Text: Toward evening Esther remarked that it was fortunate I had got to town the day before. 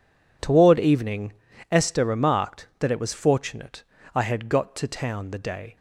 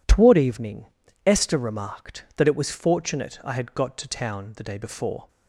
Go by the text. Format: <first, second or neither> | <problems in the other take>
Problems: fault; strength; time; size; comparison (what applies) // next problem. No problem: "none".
second | pauses between "evening" and "Esther"; slight; at 1.3 s; 0.36 s long; also in the second // pauses between "fortunate" and "I"; slight; at 3.8 s; 0.32 s long // stops before "before"; at 5.7 s